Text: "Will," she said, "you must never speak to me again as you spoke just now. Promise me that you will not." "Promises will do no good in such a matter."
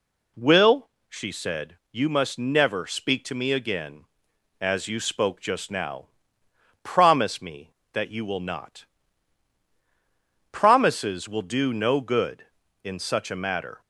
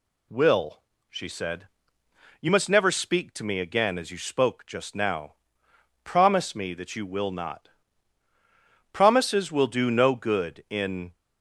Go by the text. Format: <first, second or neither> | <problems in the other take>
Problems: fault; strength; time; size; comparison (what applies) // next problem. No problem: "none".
first | stops before "such a matter"; at 11.1 s